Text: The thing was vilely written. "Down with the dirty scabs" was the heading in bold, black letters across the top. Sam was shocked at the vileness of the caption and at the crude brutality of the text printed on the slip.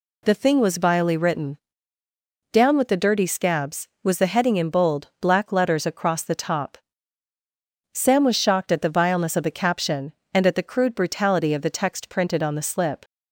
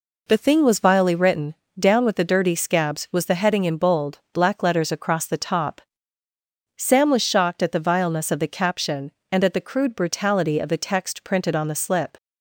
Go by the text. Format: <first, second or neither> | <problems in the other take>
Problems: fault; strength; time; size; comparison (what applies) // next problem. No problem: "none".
neither | none